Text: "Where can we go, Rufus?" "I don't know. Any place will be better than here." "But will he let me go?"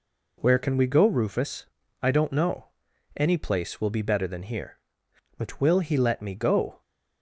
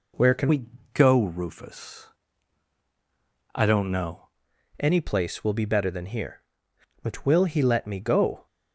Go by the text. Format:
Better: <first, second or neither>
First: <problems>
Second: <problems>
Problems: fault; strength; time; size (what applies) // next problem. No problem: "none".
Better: first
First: none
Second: changes voice from "we" to "know"; from 0.4 to 4.2 s; 3.8 s long // pauses between "we" and "go"; slight; at 0.6 s; 0.26 s long